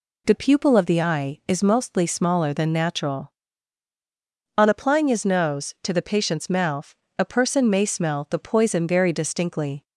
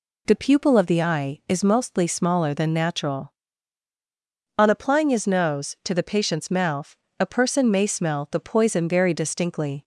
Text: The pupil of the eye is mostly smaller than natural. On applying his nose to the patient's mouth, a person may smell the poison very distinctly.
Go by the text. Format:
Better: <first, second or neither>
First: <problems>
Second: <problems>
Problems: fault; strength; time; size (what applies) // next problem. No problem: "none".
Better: neither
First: none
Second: none